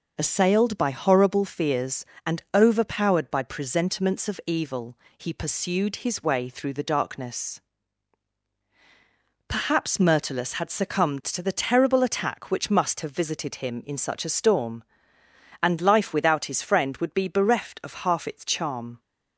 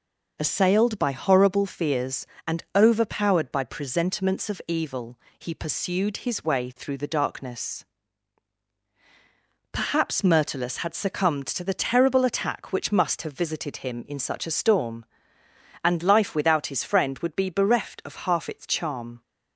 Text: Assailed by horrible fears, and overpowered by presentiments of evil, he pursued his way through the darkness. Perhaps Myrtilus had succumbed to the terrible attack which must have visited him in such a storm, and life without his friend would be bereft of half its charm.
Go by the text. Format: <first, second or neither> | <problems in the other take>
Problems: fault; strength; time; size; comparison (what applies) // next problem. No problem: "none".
neither | none